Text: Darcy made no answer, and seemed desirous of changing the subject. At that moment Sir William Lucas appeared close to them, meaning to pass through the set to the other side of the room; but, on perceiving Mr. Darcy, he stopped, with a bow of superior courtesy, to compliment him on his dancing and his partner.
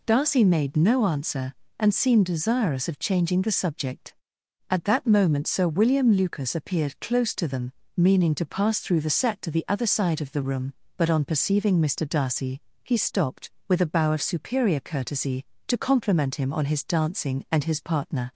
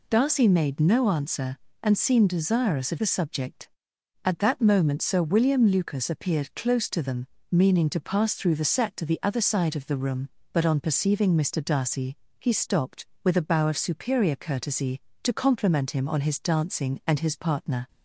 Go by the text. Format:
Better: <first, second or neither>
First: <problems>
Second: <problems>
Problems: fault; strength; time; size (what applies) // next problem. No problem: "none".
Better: first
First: none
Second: skips "changing"; at 2.9 s